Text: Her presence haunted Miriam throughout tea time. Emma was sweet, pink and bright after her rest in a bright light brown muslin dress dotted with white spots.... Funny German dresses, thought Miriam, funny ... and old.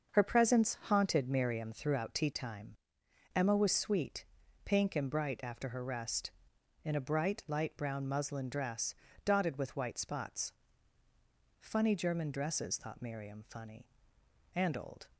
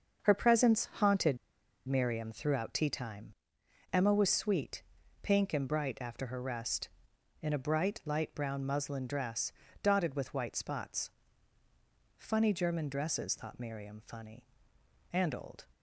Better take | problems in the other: first | starts louder than the rest; until 1.2 s; 6.5 dB; also in the first // pauses between "haunted" and "Miriam"; noticeable; at 1.3 s; 0.51 s long // pauses between "dress" and "dotted"; slight; at 9.5 s; 0.30 s long; slight in the first

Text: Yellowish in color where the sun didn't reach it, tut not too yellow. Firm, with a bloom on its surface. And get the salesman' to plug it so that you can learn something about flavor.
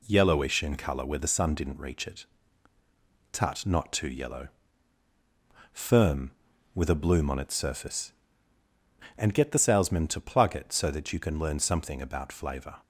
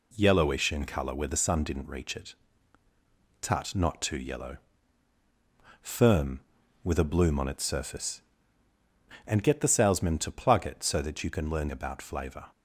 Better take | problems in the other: first | skips "something"; at 11.7 s

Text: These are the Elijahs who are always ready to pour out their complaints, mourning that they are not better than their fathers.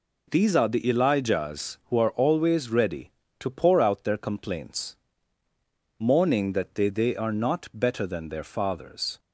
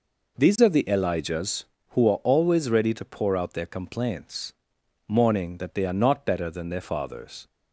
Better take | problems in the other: second | says "they" twice; at 6.8 s

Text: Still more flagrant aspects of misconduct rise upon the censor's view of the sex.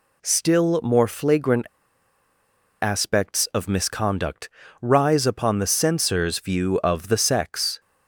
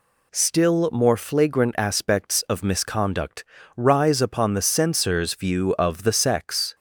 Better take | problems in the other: second | pauses between "flagrant" and "aspects"; at 1.6 s; 1.1 s long // pauses between "misconduct" and "rise"; slight; at 4.4 s; 0.32 s long; slight in the second

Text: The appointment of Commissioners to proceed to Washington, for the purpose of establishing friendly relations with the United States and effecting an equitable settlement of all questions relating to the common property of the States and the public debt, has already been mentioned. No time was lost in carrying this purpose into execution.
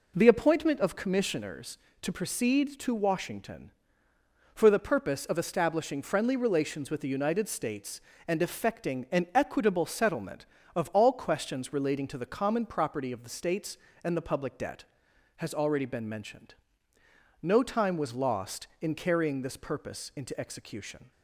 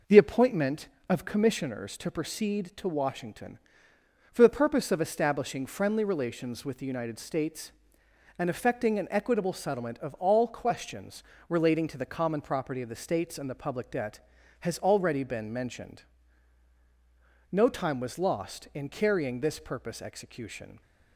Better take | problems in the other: first | pauses between "questions" and "relating"; slight; at 11.2 s; 0.26 s long // skips "into"; at 20.0 s

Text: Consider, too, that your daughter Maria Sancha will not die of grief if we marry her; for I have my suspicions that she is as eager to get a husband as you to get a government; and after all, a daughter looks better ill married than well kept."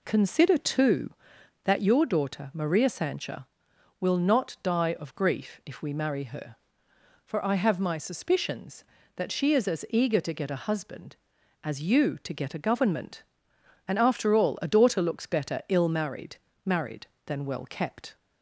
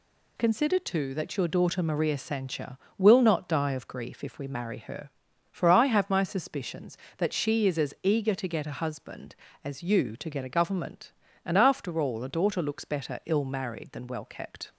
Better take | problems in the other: second | says "married" twice; at 16.6 s

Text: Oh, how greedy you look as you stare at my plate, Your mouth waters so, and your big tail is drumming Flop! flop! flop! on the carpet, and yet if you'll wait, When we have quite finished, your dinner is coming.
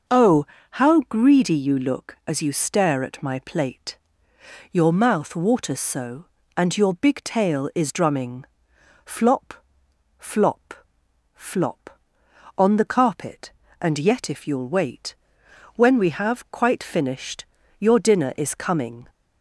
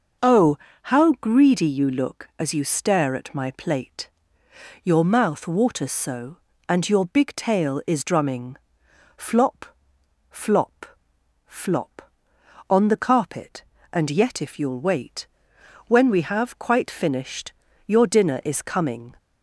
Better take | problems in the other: neither | starts louder than the rest; noticeable; the same in both // pauses between "drumming" and "Flop"; noticeable; the same in both

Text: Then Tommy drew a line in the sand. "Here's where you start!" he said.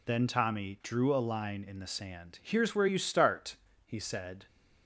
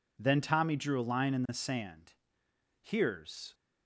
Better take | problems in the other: first | stops before "where you start he said"; at 3.5 s

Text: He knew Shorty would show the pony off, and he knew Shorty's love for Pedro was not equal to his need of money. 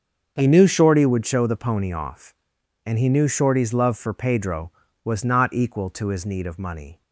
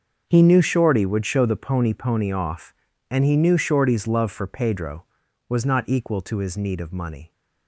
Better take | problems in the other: first | starts louder than the rest; until 1.2 s; 6.5 dB; also in the first // says "pony" twice; at 1.9 s

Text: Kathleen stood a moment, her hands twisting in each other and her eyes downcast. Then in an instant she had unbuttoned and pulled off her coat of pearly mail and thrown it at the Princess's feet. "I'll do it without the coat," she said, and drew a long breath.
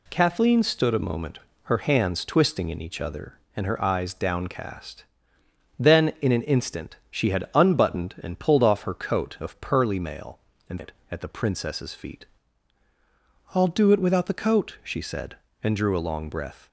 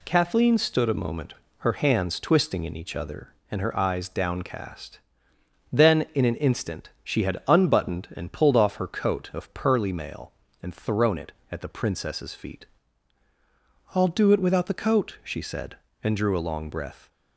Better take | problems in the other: second | skips "thrown"; at 10.7 s

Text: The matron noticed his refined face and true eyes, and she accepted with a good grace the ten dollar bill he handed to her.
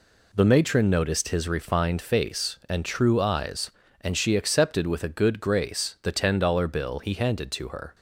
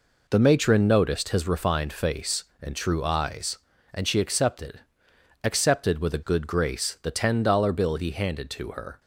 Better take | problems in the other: first | says "accepted" twice; at 5.4 s

